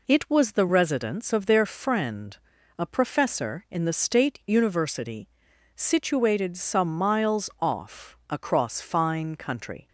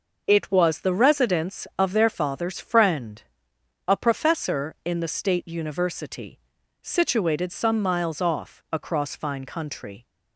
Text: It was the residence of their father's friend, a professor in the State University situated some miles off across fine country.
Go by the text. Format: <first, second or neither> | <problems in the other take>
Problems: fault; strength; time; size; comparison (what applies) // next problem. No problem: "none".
second | skips "father's"; at 1.6 s // pauses between "University" and "situated"; noticeable; at 5.2 s; 0.46 s long; also in the second